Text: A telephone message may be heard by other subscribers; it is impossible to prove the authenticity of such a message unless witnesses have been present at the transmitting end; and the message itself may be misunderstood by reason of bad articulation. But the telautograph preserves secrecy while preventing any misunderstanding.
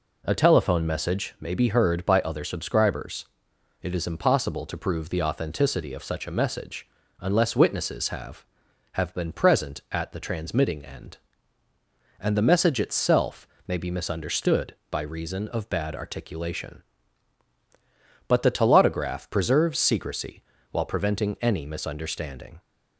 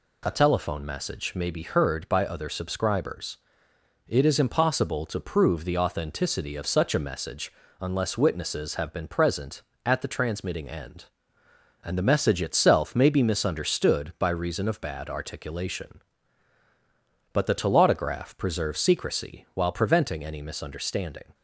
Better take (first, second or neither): second